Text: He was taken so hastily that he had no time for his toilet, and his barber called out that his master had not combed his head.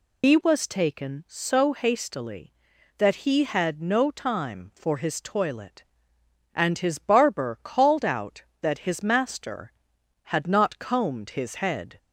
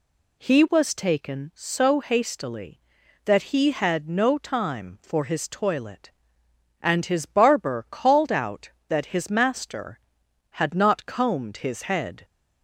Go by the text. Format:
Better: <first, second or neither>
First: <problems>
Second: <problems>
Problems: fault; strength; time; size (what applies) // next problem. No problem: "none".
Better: second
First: loses the start of "He"; at 0.2 s; 120 ms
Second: none